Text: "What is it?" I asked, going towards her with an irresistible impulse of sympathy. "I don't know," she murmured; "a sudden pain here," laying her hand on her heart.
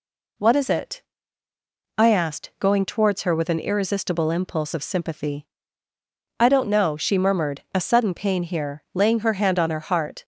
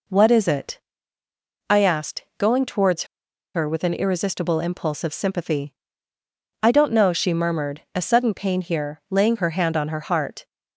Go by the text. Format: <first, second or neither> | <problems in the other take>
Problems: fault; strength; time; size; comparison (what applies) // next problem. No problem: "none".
first | pauses between "towards" and "her"; noticeable; at 3.0 s; 0.49 s long